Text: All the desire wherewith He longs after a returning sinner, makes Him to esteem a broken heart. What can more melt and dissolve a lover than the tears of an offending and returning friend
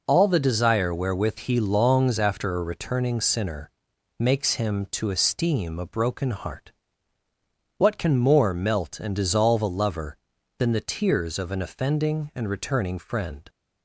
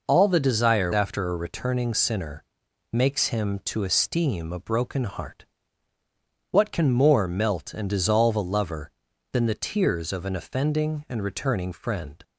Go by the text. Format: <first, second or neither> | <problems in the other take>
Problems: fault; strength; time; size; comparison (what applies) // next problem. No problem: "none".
first | skips "wherewith He longs"; at 0.9 s